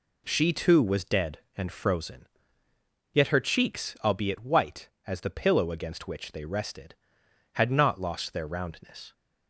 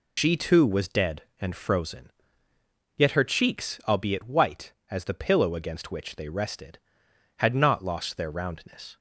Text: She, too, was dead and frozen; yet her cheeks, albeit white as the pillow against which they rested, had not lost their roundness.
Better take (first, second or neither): first